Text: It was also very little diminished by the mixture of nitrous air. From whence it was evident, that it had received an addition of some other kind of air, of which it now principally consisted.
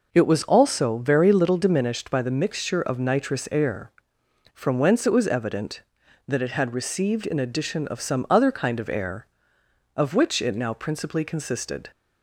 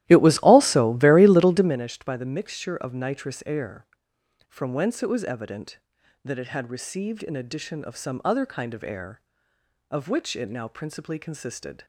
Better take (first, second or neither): first